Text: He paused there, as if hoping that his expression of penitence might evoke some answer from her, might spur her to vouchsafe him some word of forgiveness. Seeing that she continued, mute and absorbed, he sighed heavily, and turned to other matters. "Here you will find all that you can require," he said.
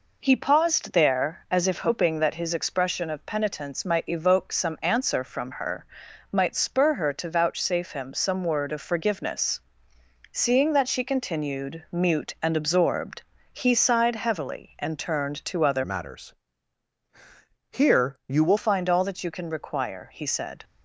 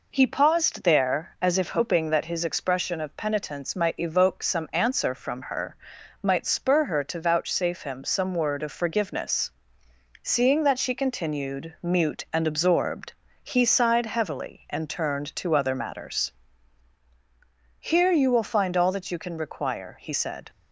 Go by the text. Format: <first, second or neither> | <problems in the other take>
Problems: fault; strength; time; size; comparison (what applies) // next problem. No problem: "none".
second | changes voice from "matters" to "will"; from 15.8 to 18.5 s; 2.7 s long